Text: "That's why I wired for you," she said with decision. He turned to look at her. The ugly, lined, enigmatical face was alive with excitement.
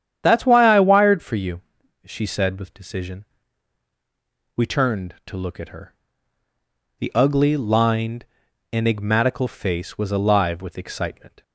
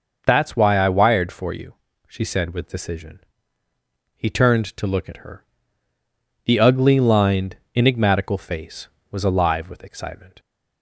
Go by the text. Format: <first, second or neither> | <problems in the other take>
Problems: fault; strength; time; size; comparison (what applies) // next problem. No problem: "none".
second | starts louder than the rest; strong; until 1.2 s; 9.5 dB // says "We" for "He"; at 4.5 s